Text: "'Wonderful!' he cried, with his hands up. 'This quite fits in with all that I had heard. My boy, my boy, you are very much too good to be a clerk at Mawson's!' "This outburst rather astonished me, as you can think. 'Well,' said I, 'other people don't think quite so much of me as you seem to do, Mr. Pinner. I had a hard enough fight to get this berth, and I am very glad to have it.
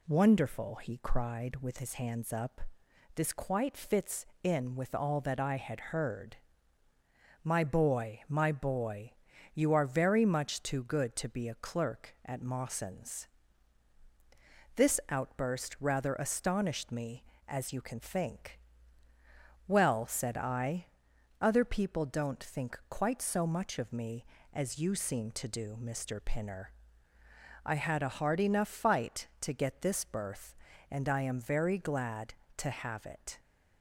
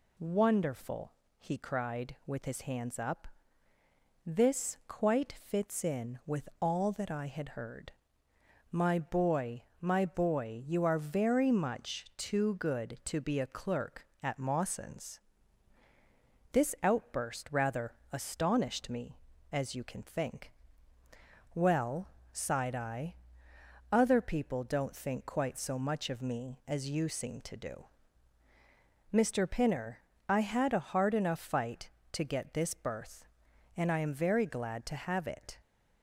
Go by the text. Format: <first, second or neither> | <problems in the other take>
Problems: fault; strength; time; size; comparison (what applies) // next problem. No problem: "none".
first | pauses between "rather" and "astonished"; slight; at 17.9 s; 0.18 s long // says "sighed" for "said"; at 22.3 s